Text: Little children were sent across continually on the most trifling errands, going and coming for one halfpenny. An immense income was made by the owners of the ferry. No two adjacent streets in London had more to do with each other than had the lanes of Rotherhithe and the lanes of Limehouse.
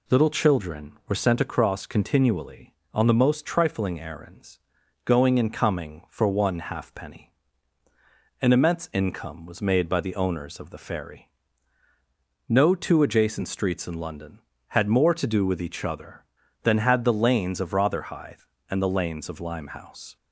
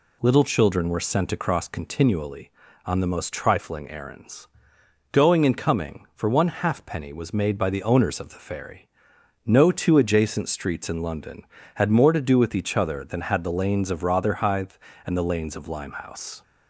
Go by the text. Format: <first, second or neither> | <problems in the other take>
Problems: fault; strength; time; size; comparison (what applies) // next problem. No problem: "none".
first | skips "An immense income"; at 7.1 s